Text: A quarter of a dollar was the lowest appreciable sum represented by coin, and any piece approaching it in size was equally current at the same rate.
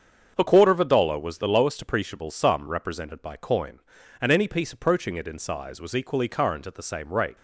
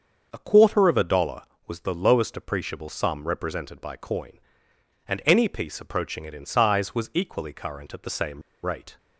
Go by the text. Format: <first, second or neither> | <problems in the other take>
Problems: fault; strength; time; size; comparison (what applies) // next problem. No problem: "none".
first | starts louder than the rest; until 1.3 s; 6.5 dB; also in the first // pauses between "same" and "rate"; slight; at 8.4 s; 0.23 s long